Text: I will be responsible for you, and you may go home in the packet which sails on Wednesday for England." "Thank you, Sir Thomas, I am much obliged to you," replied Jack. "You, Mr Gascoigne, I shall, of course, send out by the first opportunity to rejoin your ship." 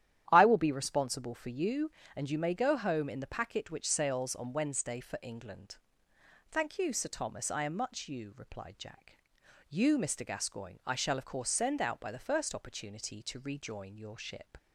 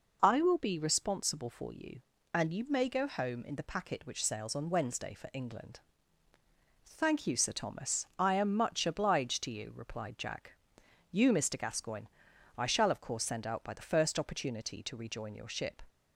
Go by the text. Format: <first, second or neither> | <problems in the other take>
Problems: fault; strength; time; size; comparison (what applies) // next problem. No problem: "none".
second | starts louder than the rest; strong; until 1.3 s; 11 dB // skips "obliged to"; at 8.0 s